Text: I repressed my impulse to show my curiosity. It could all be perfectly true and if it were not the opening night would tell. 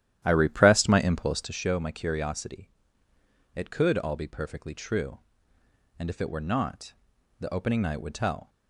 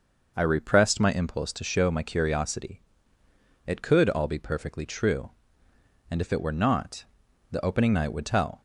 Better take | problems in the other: second | starts louder than the rest; strong; until 1.6 s; 11.5 dB // pauses between "not" and "the"; noticeable; at 6.9 s; 0.48 s long; noticeable in the second

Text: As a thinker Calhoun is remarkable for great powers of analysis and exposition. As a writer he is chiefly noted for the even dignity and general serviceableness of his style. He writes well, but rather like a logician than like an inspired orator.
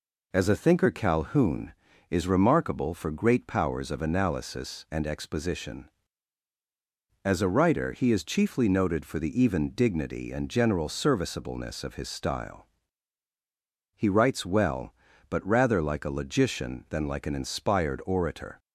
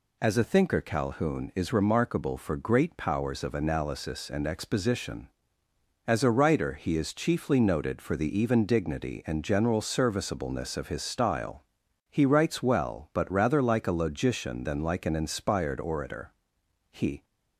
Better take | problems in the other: first | goes on to say "He"; slight; from 16.9 s on; 0.32 s long

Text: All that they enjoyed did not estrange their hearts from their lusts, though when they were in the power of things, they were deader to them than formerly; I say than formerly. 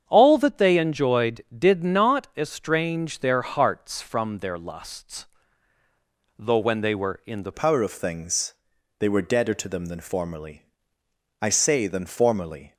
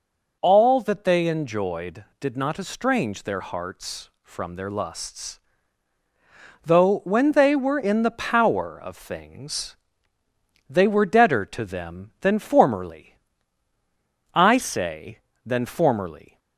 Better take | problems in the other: second | starts louder than the rest; strong; until 1.0 s; 8 dB // changes voice at "power"; from 7.5 s on; 5.2 s long

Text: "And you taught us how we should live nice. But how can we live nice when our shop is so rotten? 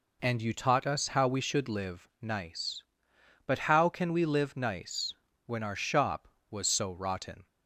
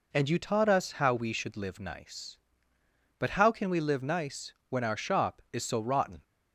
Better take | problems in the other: second | pauses between "nice" and "when"; slight; at 5.1 s; 0.32 s long; slight in the second // says "was" for "is"; at 6.5 s

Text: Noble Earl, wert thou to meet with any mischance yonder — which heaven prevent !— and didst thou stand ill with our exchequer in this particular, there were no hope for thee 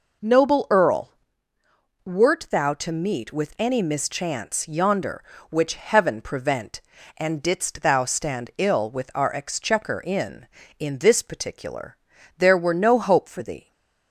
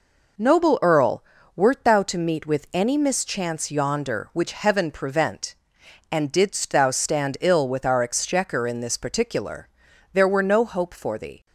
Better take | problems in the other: second | says "in" twice; at 10.7 s // stays silent after the last word; slight; from 13.5 s on; 0.6 s long

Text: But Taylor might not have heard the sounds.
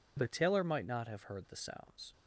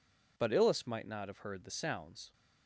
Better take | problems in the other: first | says "Illis" for "Taylor"; at 0.5 s

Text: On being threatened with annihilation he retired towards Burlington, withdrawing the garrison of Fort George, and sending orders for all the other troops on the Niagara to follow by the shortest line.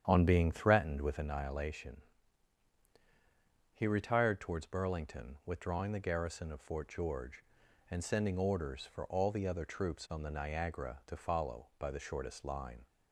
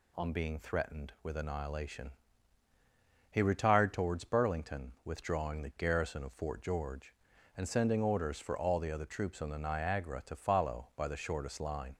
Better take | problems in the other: second | starts louder than the rest; strong; until 1.3 s; 9 dB // pauses between "annihilation" and "he"; strong; at 2.0 s; 1.7 s long; also in the second

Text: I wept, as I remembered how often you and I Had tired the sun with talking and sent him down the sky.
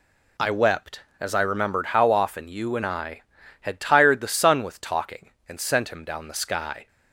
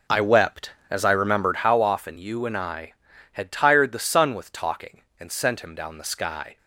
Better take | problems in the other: first | starts louder than the rest; until 1.7 s; 4 dB

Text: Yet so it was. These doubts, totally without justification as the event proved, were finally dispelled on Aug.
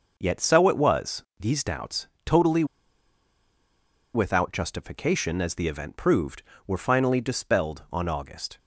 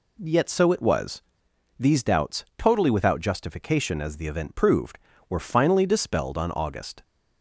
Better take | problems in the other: second | pauses between "totally" and "without"; strong; at 2.6 s; 1.4 s long

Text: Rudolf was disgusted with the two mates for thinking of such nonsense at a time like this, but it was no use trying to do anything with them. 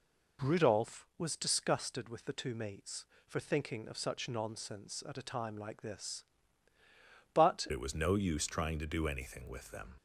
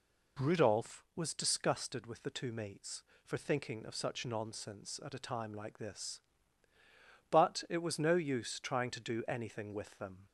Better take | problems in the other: second | changes voice at "it"; from 7.7 s on; 2.2 s long

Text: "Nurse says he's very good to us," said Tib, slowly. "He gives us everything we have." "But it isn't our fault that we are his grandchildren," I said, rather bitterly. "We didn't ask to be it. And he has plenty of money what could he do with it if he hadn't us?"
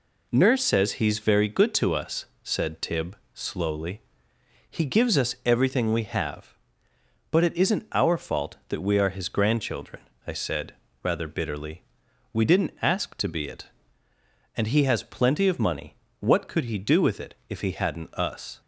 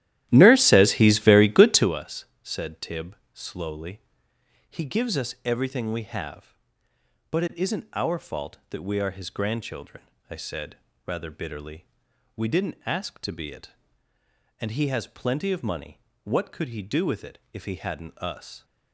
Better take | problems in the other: first | starts louder than the rest; strong; until 1.9 s; 13.5 dB // pauses between "money" and "what"; slight; at 15.9 s; 0.26 s long; slight in the first // pauses between "it" and "if"; slight; at 17.3 s; 0.16 s long; slight in the first

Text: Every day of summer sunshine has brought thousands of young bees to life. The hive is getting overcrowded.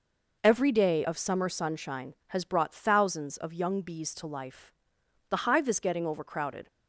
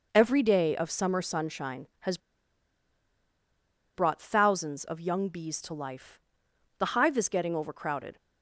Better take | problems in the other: first | pauses between "has" and "brought"; strong; at 2.1 s; 1.7 s long

